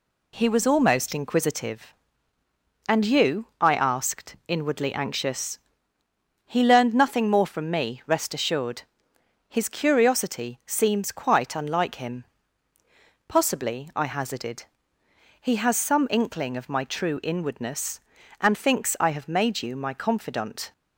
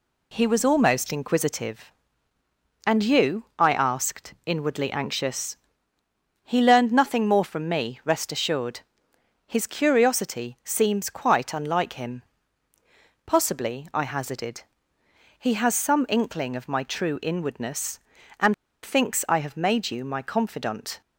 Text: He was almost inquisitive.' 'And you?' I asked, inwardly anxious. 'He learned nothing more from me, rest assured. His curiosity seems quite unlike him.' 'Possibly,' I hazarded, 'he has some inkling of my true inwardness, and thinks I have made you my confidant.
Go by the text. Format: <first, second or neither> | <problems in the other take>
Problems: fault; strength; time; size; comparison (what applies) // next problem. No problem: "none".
first | pauses between "and" and "thinks"; slight; at 18.5 s; 0.30 s long